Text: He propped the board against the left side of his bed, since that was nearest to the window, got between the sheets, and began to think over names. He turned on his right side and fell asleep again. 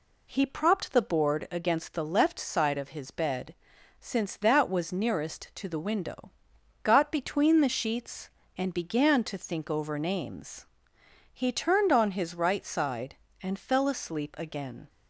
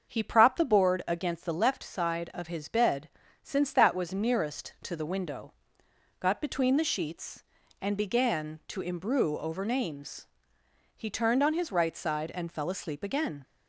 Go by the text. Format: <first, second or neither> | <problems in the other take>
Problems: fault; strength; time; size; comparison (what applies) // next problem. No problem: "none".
first | starts louder than the rest; until 1.1 s; 6.5 dB // says "imbrue" for "think"; at 8.7 s